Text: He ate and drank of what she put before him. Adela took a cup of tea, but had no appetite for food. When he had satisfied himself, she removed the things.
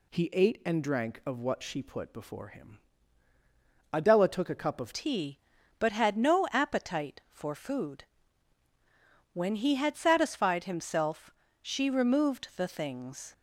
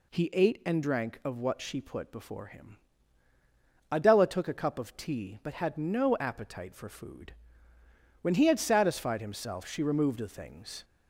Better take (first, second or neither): second